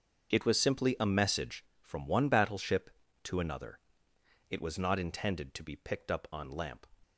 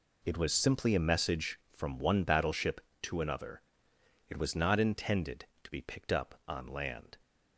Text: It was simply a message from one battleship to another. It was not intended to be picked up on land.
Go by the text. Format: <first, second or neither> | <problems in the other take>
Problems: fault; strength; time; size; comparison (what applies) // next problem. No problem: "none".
second | starts louder than the rest; until 1.3 s; 7 dB // says "lamp" for "land"; at 6.5 s